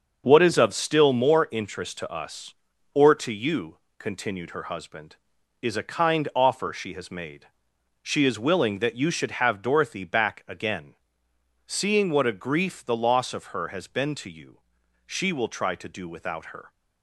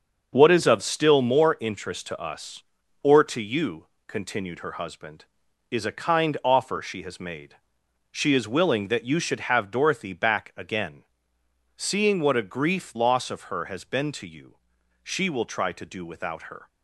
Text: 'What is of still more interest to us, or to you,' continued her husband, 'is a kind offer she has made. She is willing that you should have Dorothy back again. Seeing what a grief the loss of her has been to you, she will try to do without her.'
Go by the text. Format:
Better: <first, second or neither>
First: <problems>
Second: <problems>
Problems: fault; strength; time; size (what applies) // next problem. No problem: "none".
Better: first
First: starts louder than the rest; until 1.2 s; 6.5 dB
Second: starts louder than the rest; until 1.3 s; 6.5 dB // skips "the"; at 12.9 s